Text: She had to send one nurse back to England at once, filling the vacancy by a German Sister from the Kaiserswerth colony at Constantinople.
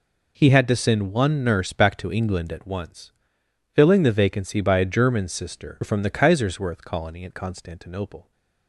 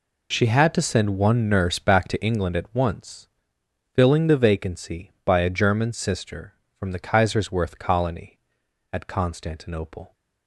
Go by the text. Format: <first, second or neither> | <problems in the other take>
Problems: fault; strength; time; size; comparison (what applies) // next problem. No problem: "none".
second | says "He" for "She"; at 0.3 s